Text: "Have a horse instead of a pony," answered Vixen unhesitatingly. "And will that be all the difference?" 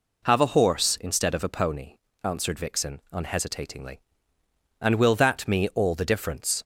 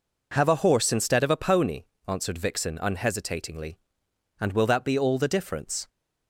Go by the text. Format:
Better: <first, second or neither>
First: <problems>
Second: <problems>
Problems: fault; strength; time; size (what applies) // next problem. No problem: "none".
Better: second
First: says "me" for "be"; at 5.4 s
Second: none